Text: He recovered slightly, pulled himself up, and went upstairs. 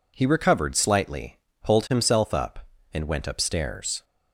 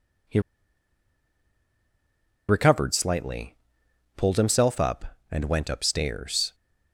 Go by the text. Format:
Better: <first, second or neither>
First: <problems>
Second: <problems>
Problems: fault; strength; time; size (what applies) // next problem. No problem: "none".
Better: first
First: none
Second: pauses between "He" and "recovered"; strong; at 0.3 s; 2.0 s long